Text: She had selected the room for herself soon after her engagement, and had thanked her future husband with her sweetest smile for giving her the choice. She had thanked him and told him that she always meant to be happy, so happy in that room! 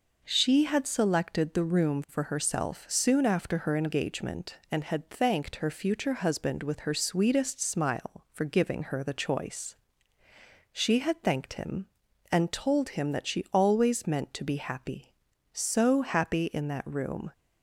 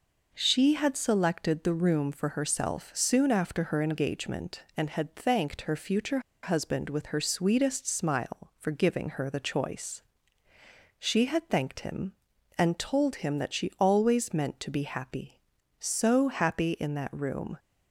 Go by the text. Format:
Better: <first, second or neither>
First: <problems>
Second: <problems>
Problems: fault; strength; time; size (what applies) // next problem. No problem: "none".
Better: first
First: none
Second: pauses between "future" and "husband"; slight; at 6.1 s; 0.23 s long